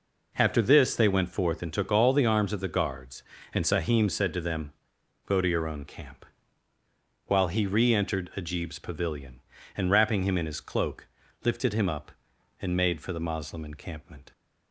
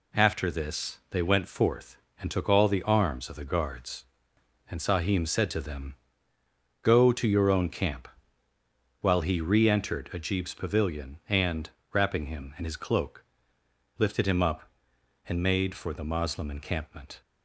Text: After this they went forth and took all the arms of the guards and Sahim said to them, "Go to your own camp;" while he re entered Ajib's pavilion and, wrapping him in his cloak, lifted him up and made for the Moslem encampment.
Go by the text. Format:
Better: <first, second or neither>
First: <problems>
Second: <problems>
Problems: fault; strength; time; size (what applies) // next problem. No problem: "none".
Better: neither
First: none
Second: none